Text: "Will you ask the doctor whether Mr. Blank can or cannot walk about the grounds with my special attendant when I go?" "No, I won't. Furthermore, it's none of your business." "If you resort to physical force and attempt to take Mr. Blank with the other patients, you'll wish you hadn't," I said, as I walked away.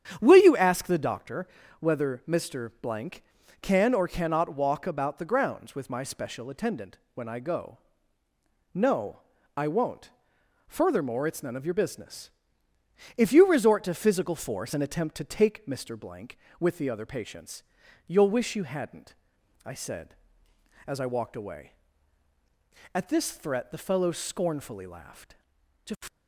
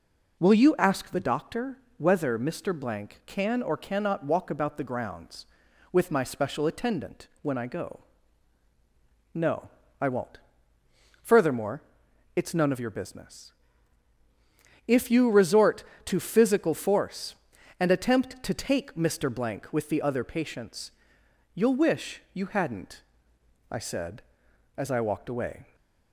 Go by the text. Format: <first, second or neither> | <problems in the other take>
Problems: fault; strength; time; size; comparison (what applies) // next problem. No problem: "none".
second | starts louder than the rest; strong; until 1.2 s; 9 dB // pauses between "doctor" and "whether"; slight; at 1.4 s; 0.34 s long; slight in the second // pauses between "attendant" and "when"; slight; at 6.9 s; 0.16 s long // goes on to say "At this threat the fellow scornfully laughed To"; strong; from 22.9 s on; 3.1 s long